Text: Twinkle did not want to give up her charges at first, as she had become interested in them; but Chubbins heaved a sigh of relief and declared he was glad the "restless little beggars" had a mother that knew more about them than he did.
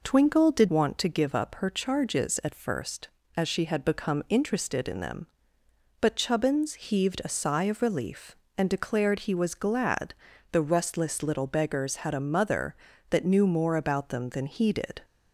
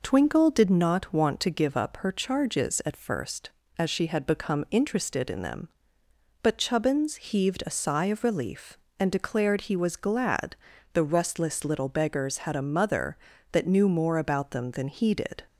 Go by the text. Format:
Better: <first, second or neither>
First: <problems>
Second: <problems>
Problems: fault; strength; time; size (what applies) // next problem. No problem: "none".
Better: second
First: skips "not"; at 0.6 s // pauses between "glad" and "the"; at 10.1 s; 0.38 s long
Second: pauses between "glad" and "the"; at 10.5 s; 0.38 s long